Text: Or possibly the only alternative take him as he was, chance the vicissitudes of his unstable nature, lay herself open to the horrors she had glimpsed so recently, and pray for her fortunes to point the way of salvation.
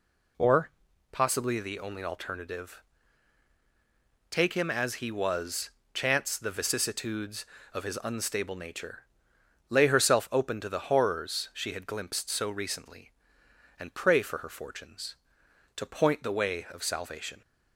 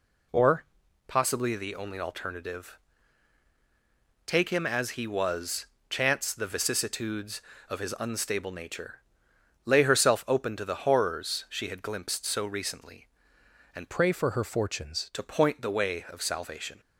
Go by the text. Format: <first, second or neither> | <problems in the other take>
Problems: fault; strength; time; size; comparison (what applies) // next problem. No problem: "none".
first | pauses between "Or" and "possibly"; at 0.6 s; 0.42 s long; also in the first // pauses between "alternative" and "take"; strong; at 2.7 s; 1.5 s long; strong in the first // changes voice from "pray" to "fortunes"; from 13.9 to 15.0 s; 1.1 s long